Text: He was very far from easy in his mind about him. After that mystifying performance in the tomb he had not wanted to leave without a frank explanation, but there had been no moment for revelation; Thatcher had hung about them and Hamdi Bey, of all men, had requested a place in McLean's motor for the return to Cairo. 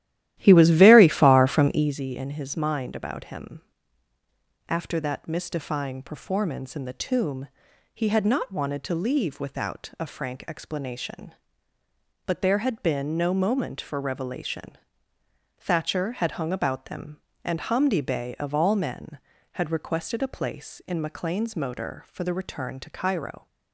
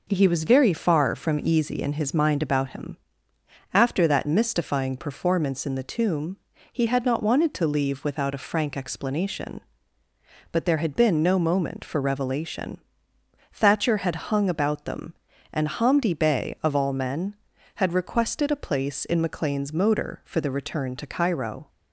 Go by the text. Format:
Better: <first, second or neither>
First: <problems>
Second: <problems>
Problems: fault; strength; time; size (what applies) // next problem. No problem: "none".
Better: second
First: starts louder than the rest; strong; until 2.0 s; 13.5 dB // pauses between "tomb" and "he"; at 7.4 s; 0.44 s long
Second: pauses between "tomb" and "he"; slight; at 6.3 s; 0.36 s long